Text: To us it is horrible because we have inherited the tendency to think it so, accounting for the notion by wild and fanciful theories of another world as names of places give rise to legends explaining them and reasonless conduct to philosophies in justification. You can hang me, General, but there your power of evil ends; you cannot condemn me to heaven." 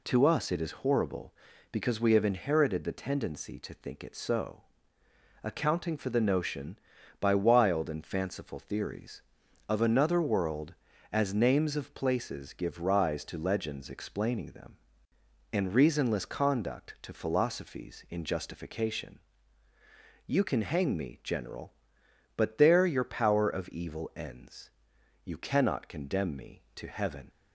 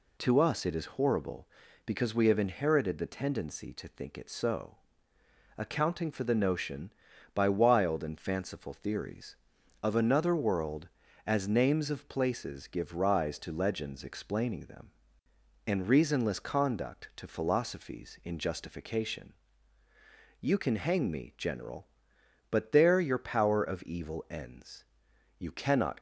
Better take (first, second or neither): first